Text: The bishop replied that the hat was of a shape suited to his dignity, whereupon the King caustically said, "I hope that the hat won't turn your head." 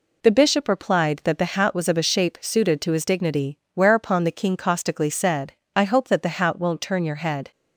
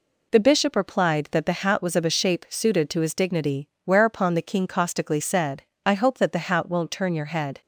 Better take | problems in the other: neither | none

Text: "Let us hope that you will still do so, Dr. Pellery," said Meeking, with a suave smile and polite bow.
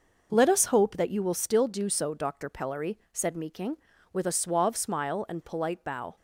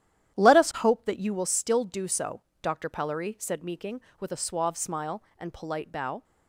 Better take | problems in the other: first | starts louder than the rest; strong; until 1.5 s; 11 dB

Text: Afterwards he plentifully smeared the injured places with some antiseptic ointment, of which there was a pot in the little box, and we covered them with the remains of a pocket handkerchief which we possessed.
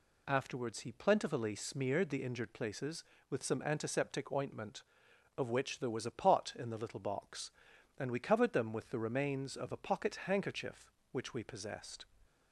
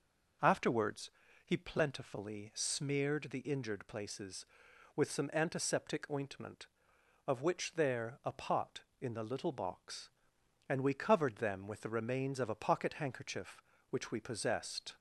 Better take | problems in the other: first | pauses between "Afterwards" and "he"; slight; at 1.1 s; 0.34 s long // skips "was"; at 8.2 s

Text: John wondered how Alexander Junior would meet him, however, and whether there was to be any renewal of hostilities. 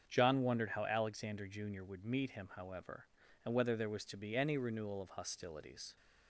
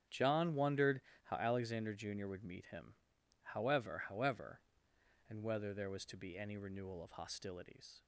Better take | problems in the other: first | starts louder than the rest; strong; until 1.3 s; 9.5 dB; strong in the first // pauses between "wondered" and "how"; slight; at 1.0 s; 0.22 s long // says "however" twice; at 4.0 s

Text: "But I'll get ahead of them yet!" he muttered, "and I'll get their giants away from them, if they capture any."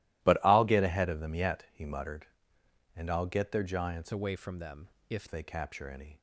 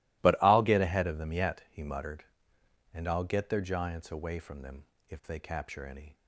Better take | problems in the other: second | changes voice from "away" to "if"; from 4.1 to 5.2 s; 1.1 s long

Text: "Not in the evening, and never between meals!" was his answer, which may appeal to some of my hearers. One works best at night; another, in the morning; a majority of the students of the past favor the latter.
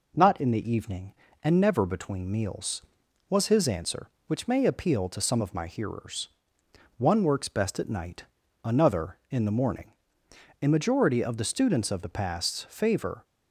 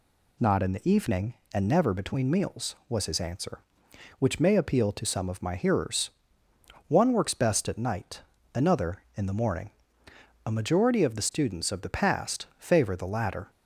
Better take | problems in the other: second | stops before "the latter"; at 13.2 s

